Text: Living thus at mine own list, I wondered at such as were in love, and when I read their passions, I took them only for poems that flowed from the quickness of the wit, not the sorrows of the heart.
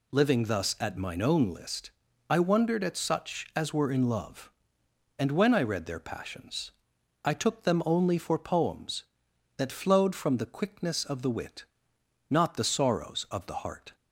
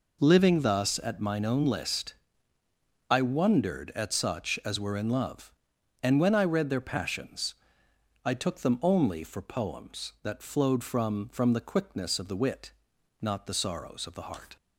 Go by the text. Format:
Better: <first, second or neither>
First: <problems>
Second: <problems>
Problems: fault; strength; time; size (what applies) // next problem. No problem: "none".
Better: first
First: none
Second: says "from" twice; at 11.2 s